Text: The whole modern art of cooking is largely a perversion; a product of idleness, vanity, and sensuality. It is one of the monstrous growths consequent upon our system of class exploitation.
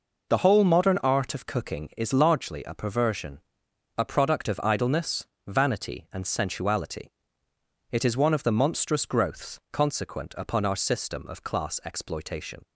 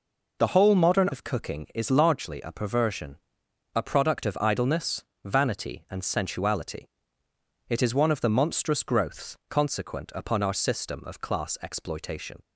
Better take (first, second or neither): first